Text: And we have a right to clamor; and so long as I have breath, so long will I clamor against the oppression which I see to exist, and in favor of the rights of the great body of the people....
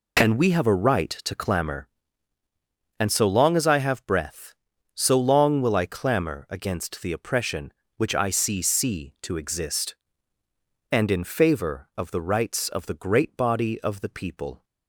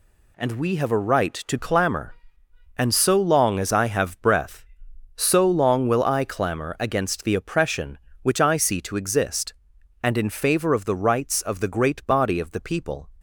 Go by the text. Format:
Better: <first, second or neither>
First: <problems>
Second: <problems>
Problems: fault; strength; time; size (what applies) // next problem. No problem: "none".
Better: second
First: says "see" twice; at 8.5 s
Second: none